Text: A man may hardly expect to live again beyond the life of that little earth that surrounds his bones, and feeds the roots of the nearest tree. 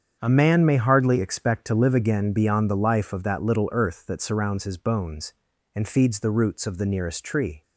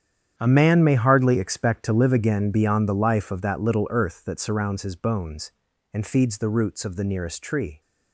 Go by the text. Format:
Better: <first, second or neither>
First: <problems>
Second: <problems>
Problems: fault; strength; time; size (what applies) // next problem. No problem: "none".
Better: first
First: starts louder than the rest; strong; until 1.2 s; 7.5 dB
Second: gets quieter; strong; throughout; 14.5 dB // starts louder than the rest; strong; until 1.3 s; 9 dB